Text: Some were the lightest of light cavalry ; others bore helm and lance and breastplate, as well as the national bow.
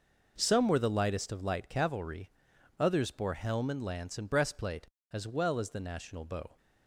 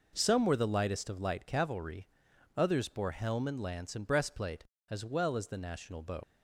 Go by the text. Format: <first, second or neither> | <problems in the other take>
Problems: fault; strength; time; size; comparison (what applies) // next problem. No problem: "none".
first | leaves "bow" unfinished; at 6.2 s; 105 ms